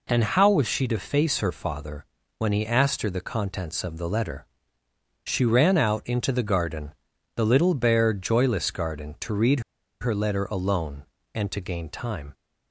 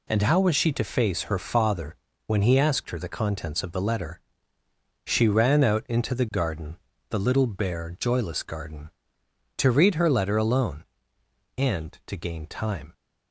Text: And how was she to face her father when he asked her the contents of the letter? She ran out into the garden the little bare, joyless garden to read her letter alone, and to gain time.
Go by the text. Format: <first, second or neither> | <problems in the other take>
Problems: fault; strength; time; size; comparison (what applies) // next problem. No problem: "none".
second | pauses between "father" and "when"; slight; at 2.0 s; 0.32 s long; slight in the second // pauses between "garden" and "the"; at 6.9 s; 0.42 s long; slight in the second // pauses between "read" and "her"; at 9.6 s; 0.40 s long